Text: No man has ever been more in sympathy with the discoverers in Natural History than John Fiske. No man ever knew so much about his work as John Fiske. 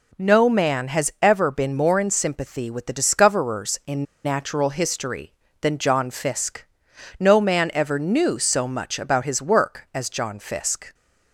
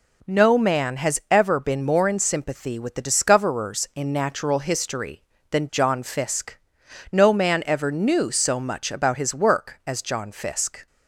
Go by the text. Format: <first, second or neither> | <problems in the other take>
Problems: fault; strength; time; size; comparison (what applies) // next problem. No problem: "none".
second | pauses between "in" and "Natural"; slight; at 4.0 s; 0.19 s long